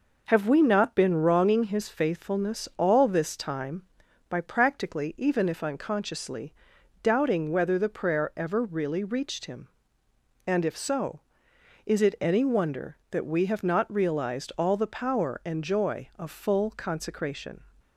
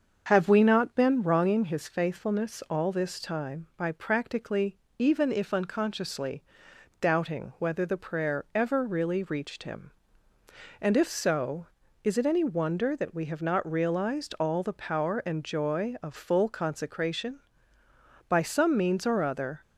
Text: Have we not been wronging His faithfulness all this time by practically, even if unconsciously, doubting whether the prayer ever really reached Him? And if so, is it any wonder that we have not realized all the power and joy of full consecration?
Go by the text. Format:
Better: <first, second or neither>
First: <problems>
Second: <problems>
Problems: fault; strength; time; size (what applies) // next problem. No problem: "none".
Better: first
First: none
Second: starts louder than the rest; until 1.2 s; 6.5 dB // goes on to say "By some means or other"; from 18.2 s on; 1.3 s long